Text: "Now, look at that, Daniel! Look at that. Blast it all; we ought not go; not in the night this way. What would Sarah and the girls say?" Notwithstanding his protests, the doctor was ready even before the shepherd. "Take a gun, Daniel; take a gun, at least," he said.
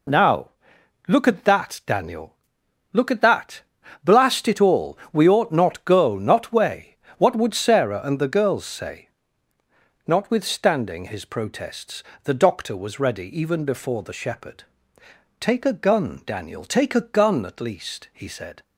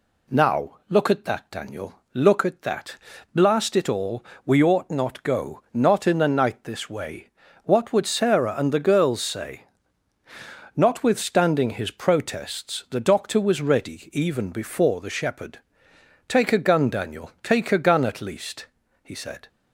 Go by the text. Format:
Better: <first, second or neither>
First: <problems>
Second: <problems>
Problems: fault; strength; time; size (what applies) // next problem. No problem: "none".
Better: second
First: skips "in the night this"; at 6.5 s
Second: none